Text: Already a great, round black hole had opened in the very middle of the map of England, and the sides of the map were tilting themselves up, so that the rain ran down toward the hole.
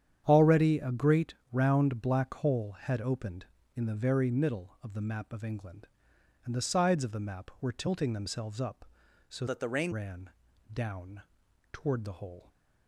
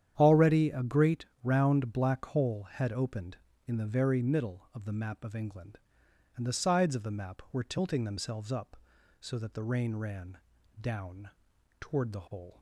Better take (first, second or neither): second